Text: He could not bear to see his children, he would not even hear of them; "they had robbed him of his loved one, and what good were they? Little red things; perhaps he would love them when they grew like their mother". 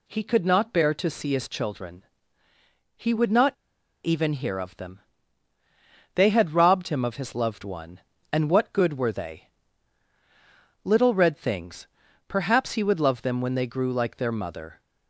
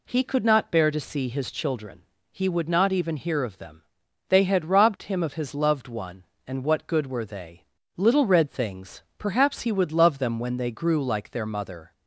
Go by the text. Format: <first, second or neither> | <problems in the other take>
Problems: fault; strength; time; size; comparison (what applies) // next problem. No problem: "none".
second | pauses between "not" and "even"; noticeable; at 3.5 s; 0.50 s long